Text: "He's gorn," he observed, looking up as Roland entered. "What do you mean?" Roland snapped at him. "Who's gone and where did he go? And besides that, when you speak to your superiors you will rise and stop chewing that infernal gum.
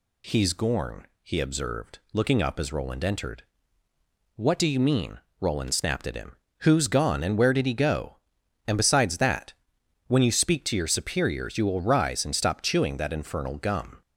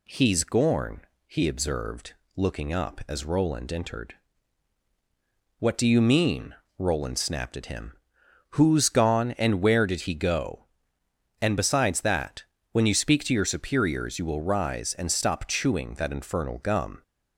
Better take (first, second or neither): neither